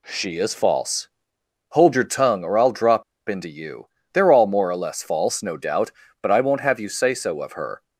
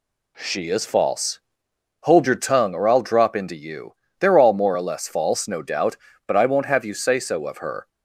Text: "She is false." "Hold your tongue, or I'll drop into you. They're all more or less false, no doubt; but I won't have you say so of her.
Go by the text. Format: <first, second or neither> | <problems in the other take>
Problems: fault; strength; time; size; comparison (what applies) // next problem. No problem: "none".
second | pauses between "drop" and "into"; slight; at 3.0 s; 0.25 s long